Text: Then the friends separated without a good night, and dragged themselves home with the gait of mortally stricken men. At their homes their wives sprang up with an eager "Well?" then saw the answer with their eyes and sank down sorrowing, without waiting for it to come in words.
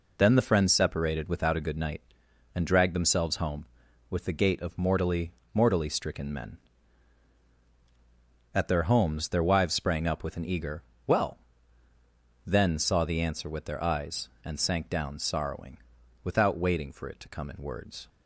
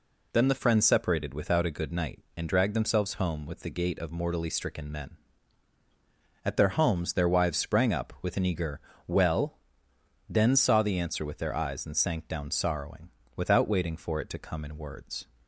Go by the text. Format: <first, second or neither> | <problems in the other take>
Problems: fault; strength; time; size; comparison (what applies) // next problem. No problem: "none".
second | says "mortally" twice; at 5.5 s // pauses between "eager" and "Well"; slight; at 10.8 s; 0.24 s long; slight in the second